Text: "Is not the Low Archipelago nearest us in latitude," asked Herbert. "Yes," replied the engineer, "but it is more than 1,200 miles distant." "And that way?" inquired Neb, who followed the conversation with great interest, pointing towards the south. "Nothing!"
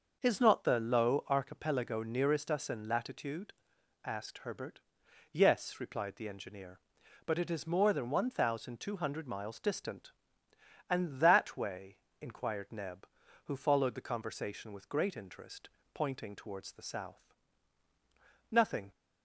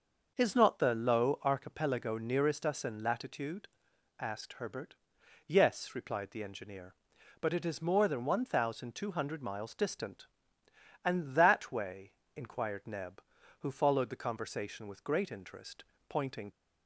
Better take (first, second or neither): first